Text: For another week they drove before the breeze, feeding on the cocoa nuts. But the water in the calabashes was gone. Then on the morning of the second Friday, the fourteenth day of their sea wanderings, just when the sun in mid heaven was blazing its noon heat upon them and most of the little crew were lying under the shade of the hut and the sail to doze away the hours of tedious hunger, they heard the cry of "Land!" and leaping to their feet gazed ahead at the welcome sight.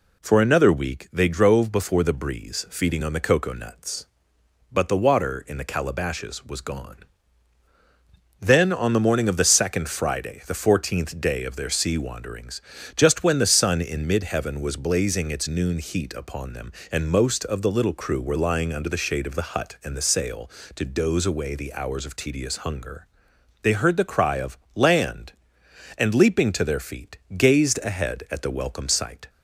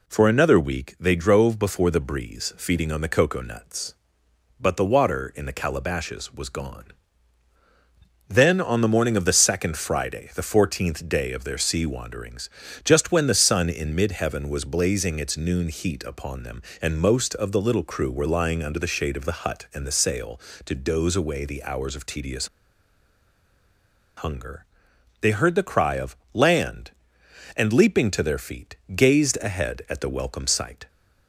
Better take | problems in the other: first | pauses between "tedious" and "hunger"; strong; at 22.4 s; 1.7 s long // pauses between "of" and "Land"; slight; at 26.1 s; 0.16 s long; slight in the first // pauses between "feet" and "gazed"; slight; at 28.7 s; 0.20 s long; slight in the first

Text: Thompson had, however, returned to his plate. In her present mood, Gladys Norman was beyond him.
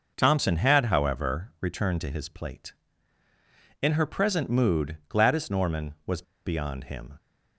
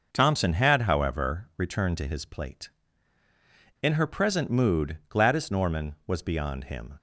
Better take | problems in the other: second | pauses between "was" and "beyond"; slight; at 6.2 s; 0.23 s long

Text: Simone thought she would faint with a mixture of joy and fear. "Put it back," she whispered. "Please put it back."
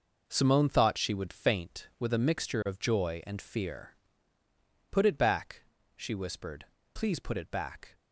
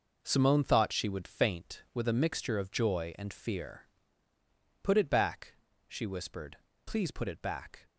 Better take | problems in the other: neither | none

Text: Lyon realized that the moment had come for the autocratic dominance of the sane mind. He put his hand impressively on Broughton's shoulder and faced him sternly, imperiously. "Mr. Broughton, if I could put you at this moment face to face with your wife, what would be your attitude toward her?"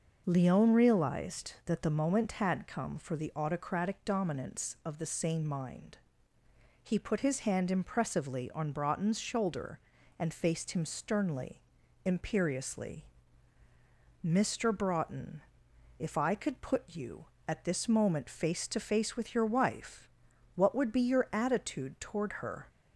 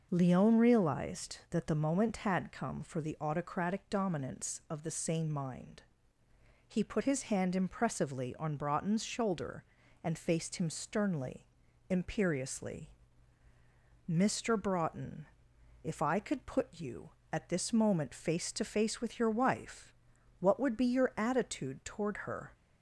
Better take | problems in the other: neither | none

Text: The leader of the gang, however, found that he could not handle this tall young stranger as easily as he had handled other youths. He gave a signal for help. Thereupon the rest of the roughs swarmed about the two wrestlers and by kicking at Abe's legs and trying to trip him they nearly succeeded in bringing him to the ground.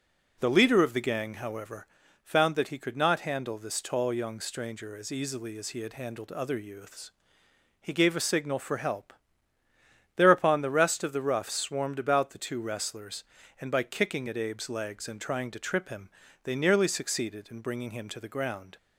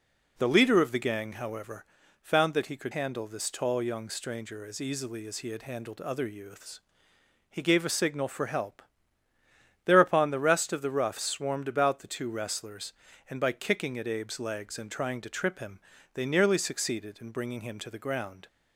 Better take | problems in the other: first | skips "not"; at 2.9 s // pauses between "him" and "they"; slight; at 15.7 s; 0.36 s long; slight in the first

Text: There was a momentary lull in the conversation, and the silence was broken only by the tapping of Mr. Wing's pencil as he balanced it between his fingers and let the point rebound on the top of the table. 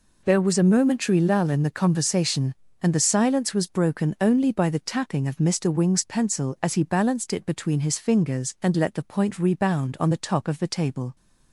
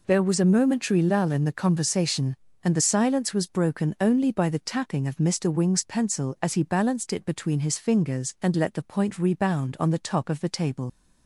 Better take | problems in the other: first | leaves "table" unfinished; at 10.8 s; 70 ms

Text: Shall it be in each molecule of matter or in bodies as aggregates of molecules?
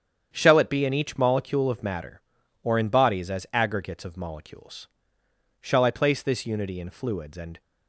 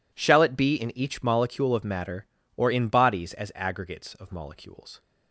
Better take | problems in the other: second | starts louder than the rest; strong; until 1.3 s; 8.5 dB // goes on to say "Shall I place this unity in fluids and"; strong; from 5.6 s on; 2.0 s long

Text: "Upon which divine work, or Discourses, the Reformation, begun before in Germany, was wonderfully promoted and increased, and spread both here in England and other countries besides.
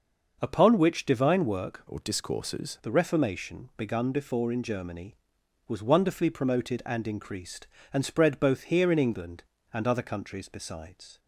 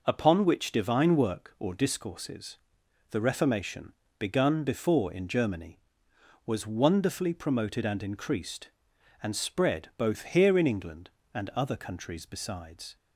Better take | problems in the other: second | starts louder than the rest; noticeable; until 1.4 s; 6 dB // changes voice from "or" to "Discourses"; from 1.8 to 2.7 s; 0.9 s long

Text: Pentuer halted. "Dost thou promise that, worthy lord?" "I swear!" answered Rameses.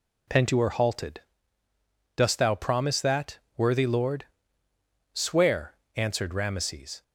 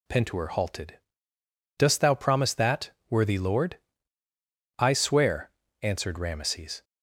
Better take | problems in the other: second | skips "I"; at 4.6 s

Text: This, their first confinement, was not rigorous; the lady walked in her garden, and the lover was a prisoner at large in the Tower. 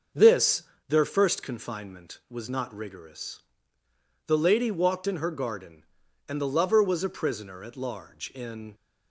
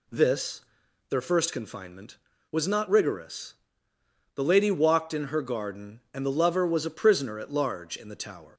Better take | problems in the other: second | starts louder than the rest; until 1.4 s; 6.5 dB // stops before "the Tower"; at 8.7 s

